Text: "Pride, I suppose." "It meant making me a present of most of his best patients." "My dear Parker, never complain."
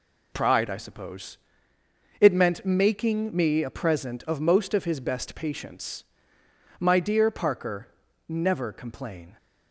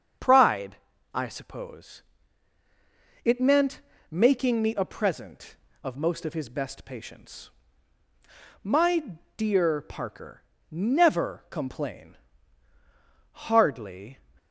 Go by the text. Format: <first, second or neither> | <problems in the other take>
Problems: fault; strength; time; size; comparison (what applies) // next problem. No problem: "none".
first | starts louder than the rest; strong; until 1.5 s; 7.5 dB // pauses between "meant" and "making"; slight; at 3.8 s; 0.28 s long // pauses between "My" and "dear"; slight; at 9.1 s; 0.18 s long // goes on to say "Hardly"; noticeable; from 13.3 s on; 0.86 s long